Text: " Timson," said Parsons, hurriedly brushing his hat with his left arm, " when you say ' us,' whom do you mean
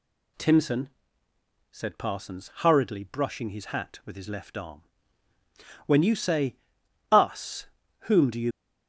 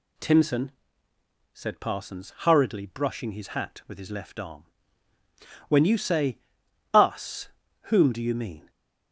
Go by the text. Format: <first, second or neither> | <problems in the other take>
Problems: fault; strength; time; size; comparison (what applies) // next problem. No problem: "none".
second | stops before "mean"; at 8.5 s